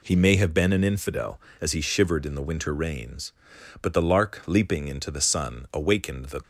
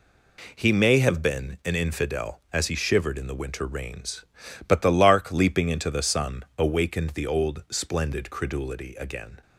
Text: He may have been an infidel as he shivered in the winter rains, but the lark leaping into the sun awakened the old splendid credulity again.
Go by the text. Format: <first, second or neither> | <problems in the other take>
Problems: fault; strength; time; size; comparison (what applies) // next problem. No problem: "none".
second | stops before "old splendid credulity again"; at 6.4 s